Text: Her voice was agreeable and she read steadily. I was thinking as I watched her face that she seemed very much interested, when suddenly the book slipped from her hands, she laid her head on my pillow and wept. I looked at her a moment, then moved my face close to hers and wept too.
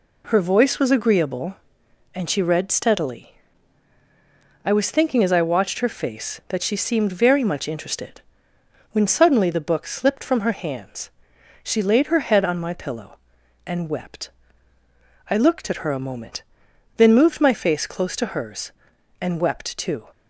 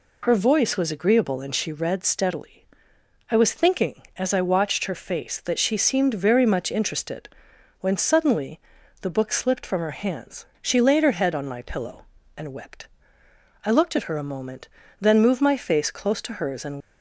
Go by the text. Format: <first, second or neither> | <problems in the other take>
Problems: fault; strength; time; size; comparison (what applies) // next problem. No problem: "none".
first | pauses between "suddenly" and "the"; at 8.5 s; 0.44 s long // stops before "wept too"; at 16.7 s